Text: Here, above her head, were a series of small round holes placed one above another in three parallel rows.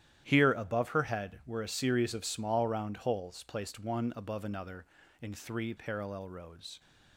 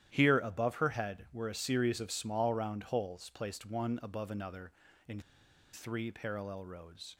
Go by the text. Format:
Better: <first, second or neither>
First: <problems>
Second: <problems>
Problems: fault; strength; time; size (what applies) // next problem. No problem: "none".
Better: first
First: starts louder than the rest; strong; until 1.2 s; 11.5 dB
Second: starts louder than the rest; strong; until 1.1 s; 11.5 dB // pauses between "in" and "three"; noticeable; at 5.2 s; 0.51 s long